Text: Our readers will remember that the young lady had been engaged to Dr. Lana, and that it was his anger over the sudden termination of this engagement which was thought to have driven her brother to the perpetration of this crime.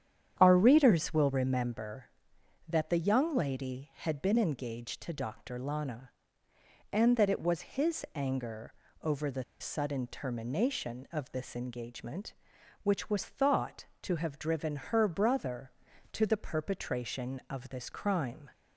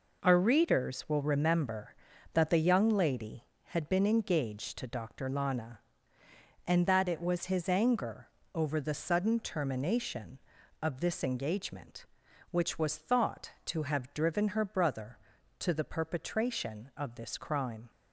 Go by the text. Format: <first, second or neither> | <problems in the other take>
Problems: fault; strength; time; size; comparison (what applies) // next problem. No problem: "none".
second | starts louder than the rest; strong; until 1.4 s; 9.5 dB // pauses between "anger" and "over"; slight; at 8.7 s; 0.30 s long; slight in the second // pauses between "the" and "sudden"; slight; at 9.4 s; 0.16 s long